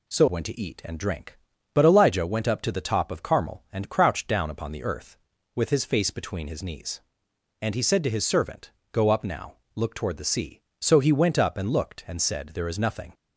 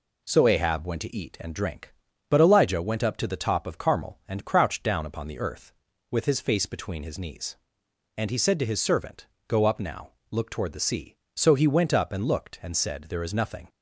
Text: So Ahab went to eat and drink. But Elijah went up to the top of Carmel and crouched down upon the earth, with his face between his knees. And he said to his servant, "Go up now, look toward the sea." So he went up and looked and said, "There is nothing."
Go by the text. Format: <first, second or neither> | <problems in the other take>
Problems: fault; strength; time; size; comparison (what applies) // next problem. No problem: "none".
second | skips "Ahab"; at 0.2 s